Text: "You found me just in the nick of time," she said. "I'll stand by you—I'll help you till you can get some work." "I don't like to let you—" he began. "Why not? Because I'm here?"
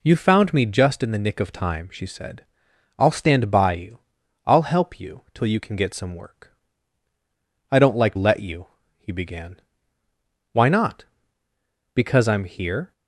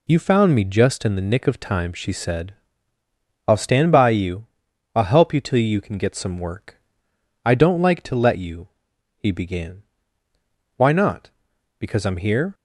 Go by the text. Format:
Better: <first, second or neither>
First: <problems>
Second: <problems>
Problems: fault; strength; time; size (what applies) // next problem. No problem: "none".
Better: second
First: skips "to"; at 8.1 s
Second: none